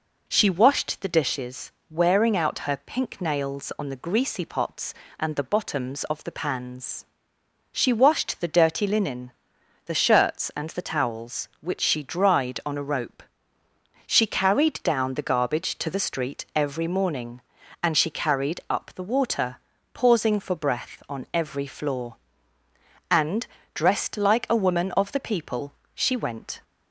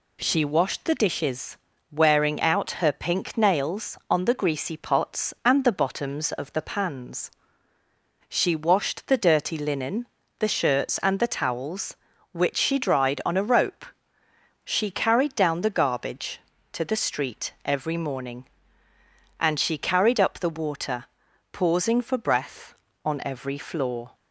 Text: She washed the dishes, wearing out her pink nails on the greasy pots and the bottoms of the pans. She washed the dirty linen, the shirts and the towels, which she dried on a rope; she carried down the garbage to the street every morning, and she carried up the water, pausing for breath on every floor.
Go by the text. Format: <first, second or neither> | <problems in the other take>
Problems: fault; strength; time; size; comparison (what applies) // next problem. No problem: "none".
second | goes on to say "And dressed like a woman of the people she went"; strong; from 23.0 s on; 3.5 s long